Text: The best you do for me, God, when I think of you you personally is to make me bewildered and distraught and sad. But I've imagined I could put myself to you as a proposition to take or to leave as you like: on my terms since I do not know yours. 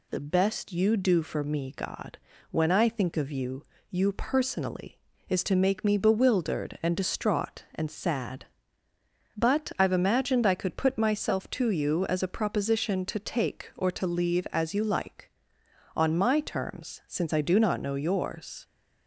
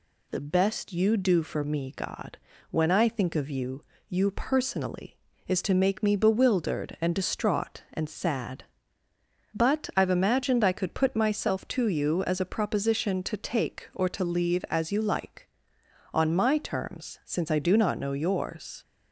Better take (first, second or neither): neither